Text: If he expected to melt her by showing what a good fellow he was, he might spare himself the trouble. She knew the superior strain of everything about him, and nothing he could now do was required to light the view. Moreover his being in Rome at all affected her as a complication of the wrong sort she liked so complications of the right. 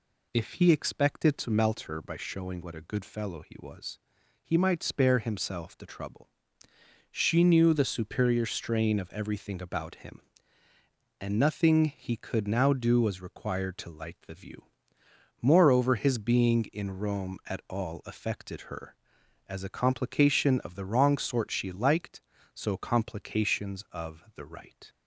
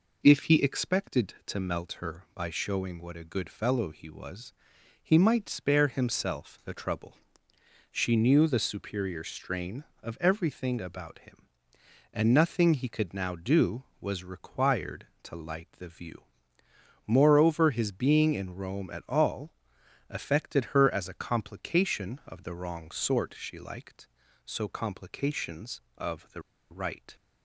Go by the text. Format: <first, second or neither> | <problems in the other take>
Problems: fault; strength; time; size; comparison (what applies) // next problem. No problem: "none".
first | pauses between "all" and "affected"; noticeable; at 19.5 s; 0.58 s long // pauses between "the" and "right"; slight; at 26.4 s; 0.29 s long